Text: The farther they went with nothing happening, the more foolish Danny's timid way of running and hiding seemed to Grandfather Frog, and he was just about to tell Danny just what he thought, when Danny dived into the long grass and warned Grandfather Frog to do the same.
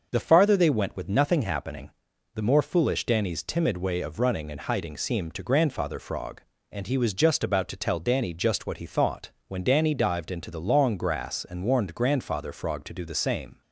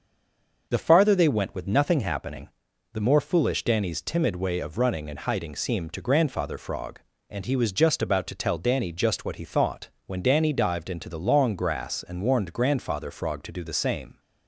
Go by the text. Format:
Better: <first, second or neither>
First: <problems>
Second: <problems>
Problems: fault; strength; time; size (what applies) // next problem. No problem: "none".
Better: first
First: starts louder than the rest; noticeable; until 1.1 s; 6 dB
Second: stays silent before the first word; slight; until 0.6 s; 0.6 s long // starts louder than the rest; noticeable; until 1.7 s; 6 dB